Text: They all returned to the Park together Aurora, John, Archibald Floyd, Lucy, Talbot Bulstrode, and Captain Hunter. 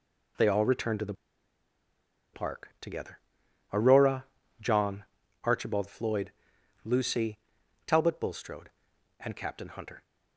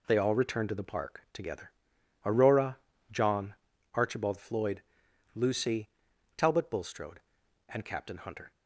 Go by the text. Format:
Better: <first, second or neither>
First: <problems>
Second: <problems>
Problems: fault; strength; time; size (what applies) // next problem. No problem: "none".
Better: second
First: pauses between "the" and "Park"; at 1.1 s; 1.2 s long // pauses between "together" and "Aurora"; noticeable; at 3.1 s; 0.54 s long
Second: pauses between "together" and "Aurora"; noticeable; at 1.7 s; 0.54 s long